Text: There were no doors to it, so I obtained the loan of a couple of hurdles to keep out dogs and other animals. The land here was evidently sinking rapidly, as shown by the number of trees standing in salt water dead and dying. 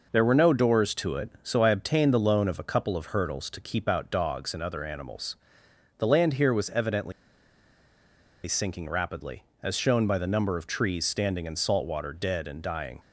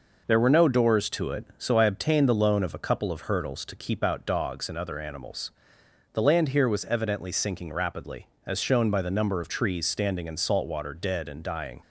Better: second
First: pauses between "evidently" and "sinking"; strong; at 7.1 s; 1.3 s long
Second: none

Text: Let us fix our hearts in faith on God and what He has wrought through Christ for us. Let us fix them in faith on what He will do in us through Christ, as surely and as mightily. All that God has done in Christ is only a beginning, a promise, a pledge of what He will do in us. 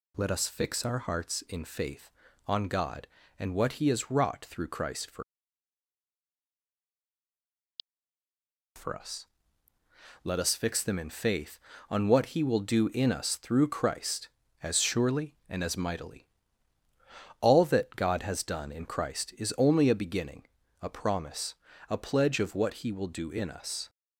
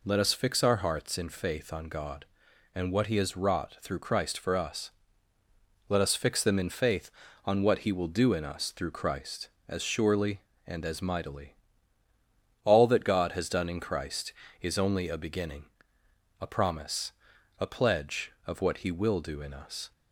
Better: second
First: says "for" twice; at 8.7 s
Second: none

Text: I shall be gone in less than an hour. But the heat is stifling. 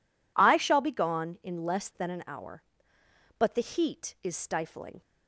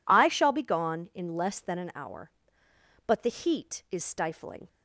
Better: neither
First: none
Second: none

